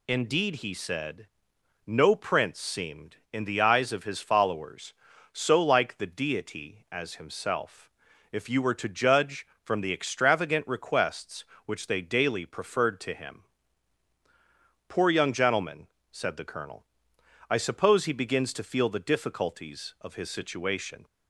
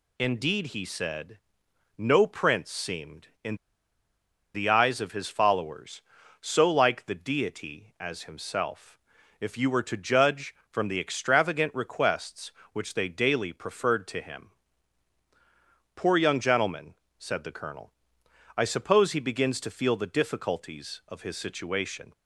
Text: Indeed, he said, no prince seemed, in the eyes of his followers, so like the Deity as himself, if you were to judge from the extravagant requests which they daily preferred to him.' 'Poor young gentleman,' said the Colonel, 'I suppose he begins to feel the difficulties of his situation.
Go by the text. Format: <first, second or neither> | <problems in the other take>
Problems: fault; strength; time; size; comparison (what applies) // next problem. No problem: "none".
first | pauses between "in" and "the"; at 3.5 s; 0.99 s long